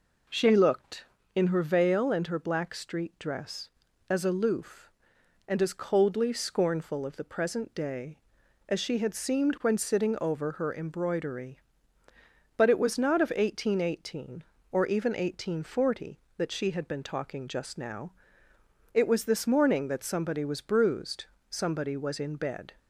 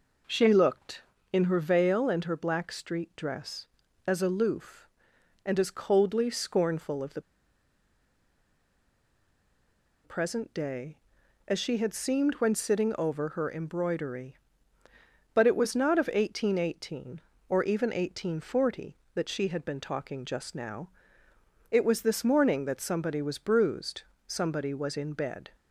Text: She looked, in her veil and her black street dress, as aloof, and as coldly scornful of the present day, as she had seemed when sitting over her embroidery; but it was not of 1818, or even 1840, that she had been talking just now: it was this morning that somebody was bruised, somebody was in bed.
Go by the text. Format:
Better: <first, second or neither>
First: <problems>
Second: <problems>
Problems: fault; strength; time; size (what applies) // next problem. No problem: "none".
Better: first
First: none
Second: pauses between "the" and "present"; strong; at 7.2 s; 2.8 s long